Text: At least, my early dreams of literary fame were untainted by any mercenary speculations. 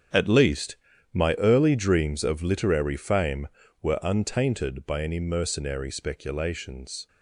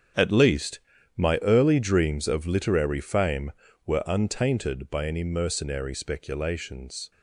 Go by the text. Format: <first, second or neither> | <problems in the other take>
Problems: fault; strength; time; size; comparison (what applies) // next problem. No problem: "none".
neither | starts louder than the rest; strong; the same in both